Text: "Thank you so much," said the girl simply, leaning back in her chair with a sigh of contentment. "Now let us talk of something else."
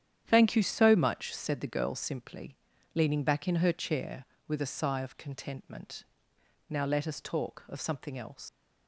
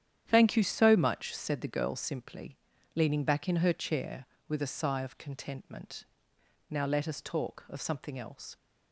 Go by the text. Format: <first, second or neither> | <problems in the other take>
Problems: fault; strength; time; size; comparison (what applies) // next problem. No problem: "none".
second | starts louder than the rest; strong; until 1.2 s; 9.5 dB; strong in the second // leaves "else" unfinished; at 8.4 s; 65 ms